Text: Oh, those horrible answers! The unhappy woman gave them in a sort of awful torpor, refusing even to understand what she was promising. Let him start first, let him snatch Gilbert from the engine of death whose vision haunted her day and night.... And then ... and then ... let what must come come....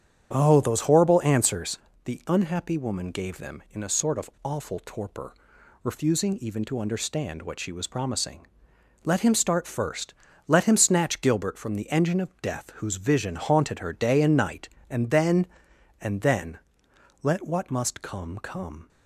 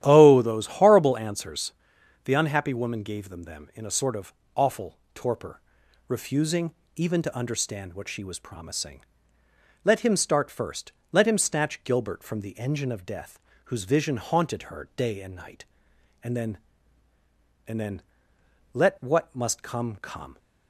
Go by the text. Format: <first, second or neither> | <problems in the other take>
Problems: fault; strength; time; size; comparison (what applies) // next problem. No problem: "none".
first | starts louder than the rest; strong; until 1.0 s; 11.5 dB; strong in the first // says "them" twice; at 3.4 s // pauses between "of" and "awful"; slight; at 4.3 s; 0.24 s long // pauses between "awful" and "torpor"; slight; at 4.9 s; 0.16 s long // pauses between "refusing" and "even"; slight; at 6.7 s; 0.22 s long // pauses between "death" and "whose"; slight; at 13.3 s; 0.28 s long